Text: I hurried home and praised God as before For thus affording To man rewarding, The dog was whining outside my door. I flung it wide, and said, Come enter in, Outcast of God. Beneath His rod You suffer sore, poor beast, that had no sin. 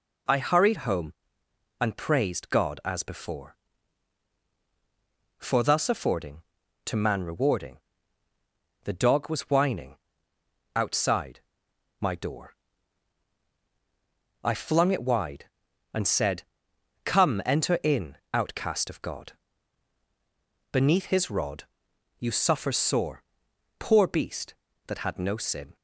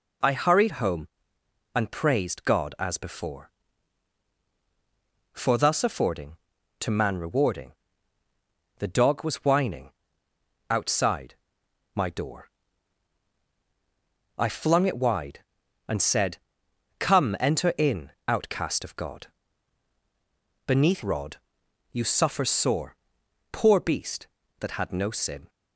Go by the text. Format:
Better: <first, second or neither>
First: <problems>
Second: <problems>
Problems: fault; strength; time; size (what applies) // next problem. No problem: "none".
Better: first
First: pauses between "whining" and "outside"; noticeable; at 9.9 s; 0.78 s long // pauses between "outside" and "my"; noticeable; at 11.4 s; 0.60 s long // pauses between "rod" and "You"; noticeable; at 21.6 s; 0.54 s long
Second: pauses between "whining" and "outside"; noticeable; at 9.9 s; 0.78 s long // pauses between "outside" and "my"; noticeable; at 11.3 s; 0.60 s long // skips "His"; at 21.0 s // pauses between "rod" and "You"; noticeable; at 21.3 s; 0.54 s long